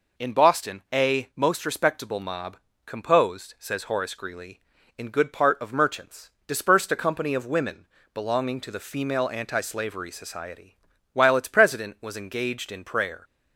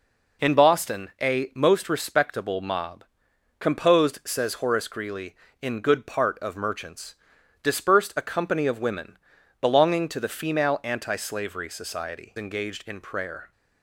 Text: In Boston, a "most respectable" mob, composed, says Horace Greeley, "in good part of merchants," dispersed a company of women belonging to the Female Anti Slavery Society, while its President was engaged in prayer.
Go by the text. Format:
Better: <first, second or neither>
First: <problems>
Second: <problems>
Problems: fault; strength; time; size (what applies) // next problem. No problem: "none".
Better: first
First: pauses between "women" and "belonging"; slight; at 7.8 s; 0.28 s long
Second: pauses between "women" and "belonging"; at 9.1 s; 0.42 s long // skips "while its President was"; at 12.3 s